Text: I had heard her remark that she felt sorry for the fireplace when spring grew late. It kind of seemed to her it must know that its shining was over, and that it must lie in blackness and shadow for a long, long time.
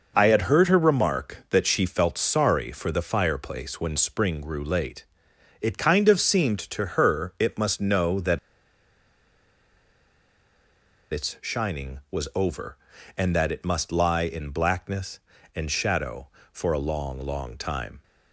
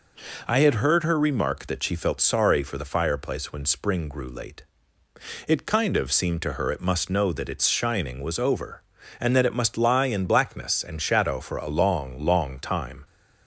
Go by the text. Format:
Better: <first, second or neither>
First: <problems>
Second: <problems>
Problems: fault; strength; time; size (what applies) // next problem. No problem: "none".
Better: second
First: pauses between "that" and "its"; strong; at 8.3 s; 2.7 s long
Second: none